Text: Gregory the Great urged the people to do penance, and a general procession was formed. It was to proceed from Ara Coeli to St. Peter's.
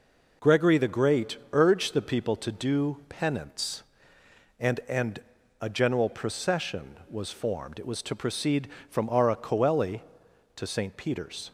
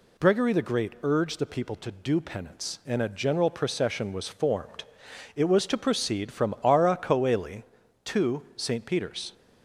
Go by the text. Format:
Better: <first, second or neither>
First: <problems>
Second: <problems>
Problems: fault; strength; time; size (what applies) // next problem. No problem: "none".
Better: second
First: pauses between "Great" and "urged"; slight; at 1.3 s; 0.16 s long // says "and" twice; at 4.8 s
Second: none